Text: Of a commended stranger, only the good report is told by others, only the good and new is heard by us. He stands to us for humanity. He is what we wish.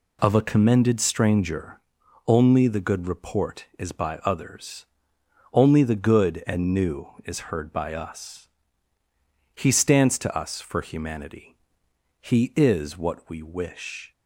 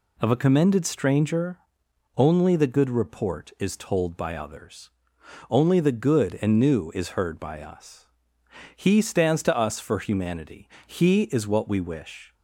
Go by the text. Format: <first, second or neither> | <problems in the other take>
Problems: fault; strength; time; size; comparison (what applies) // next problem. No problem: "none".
second | skips "told"; at 3.9 s